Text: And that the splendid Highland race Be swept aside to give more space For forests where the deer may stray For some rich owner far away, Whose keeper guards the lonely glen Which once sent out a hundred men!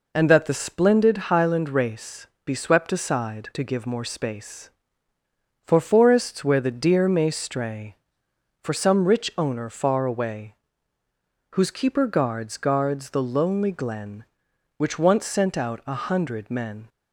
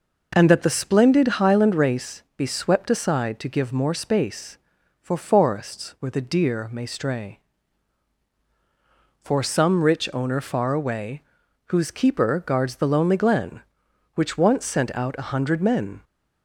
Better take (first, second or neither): second